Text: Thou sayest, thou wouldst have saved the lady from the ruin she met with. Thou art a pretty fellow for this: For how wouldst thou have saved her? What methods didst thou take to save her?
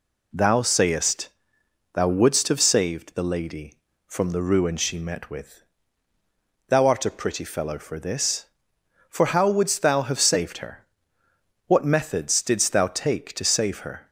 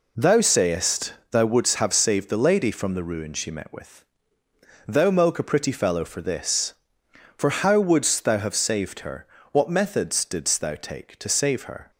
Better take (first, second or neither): first